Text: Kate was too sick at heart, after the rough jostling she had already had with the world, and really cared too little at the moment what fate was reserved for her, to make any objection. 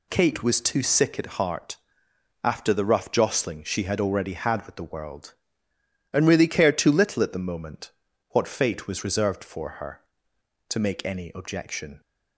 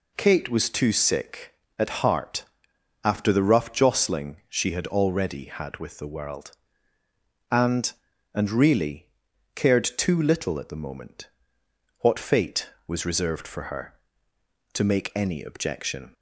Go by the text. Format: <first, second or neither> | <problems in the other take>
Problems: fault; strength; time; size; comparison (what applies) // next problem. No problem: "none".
first | says "and" twice; at 8.3 s // pauses between "really" and "cared"; noticeable; at 9.0 s; 0.48 s long // pauses between "moment" and "what"; noticeable; at 11.2 s; 0.70 s long; also in the first